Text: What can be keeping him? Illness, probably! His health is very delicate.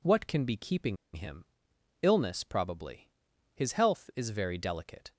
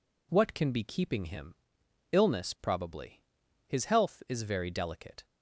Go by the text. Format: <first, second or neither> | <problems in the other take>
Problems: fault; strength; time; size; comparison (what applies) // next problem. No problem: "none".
second | pauses between "keeping" and "him"; slight; at 0.9 s; 0.19 s long